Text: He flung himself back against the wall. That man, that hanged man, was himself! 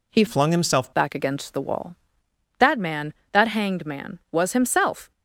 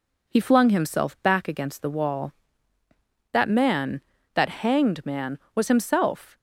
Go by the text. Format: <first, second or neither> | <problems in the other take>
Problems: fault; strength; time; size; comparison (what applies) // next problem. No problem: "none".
second | changes voice from "flung" to "himself"; from 0.2 to 0.9 s; 0.7 s long